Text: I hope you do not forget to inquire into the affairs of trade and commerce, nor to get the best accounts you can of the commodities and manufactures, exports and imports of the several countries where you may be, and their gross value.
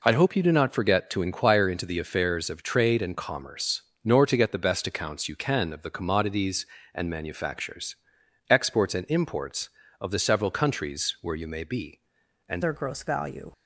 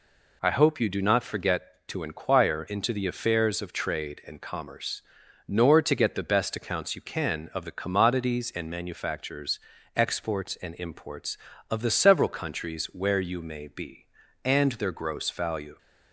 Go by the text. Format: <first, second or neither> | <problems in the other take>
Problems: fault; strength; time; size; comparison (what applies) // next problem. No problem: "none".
second | changes voice at "their"; from 12.6 s on; 0.9 s long